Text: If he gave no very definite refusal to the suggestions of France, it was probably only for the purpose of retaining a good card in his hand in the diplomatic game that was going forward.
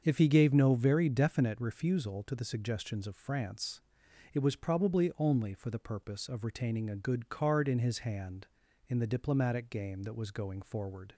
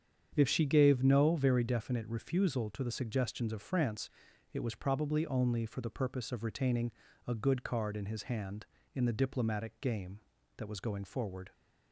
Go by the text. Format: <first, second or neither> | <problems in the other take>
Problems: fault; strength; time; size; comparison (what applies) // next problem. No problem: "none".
first | starts louder than the rest; strong; until 1.3 s; 8 dB; also in the first // says "she" for "he"; at 0.4 s // pauses between "retaining" and "a"; slight; at 6.9 s; 0.36 s long